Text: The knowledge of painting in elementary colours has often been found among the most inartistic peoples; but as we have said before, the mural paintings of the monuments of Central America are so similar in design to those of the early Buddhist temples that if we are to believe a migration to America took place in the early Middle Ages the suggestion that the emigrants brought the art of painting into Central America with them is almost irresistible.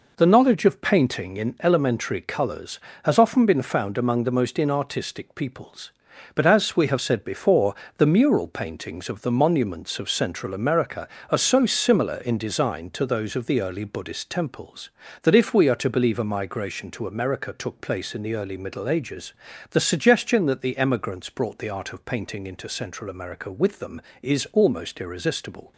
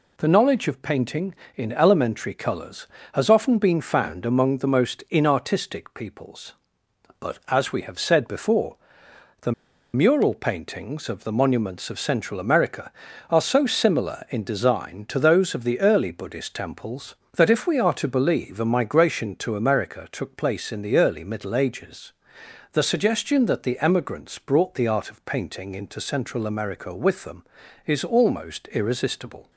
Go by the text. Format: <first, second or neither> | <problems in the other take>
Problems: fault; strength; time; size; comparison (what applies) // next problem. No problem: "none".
first | pauses between "the" and "mural"; at 9.5 s; 0.41 s long // pauses between "Ages" and "the"; noticeable; at 22.1 s; 0.60 s long; also in the first